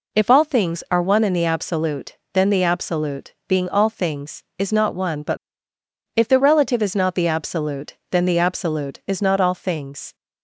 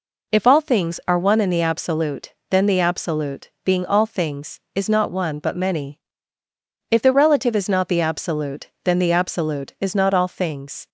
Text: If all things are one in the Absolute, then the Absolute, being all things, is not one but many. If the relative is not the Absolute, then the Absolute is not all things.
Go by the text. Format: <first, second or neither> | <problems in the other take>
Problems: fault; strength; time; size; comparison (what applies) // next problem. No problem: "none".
second | skips "many"; at 5.7 s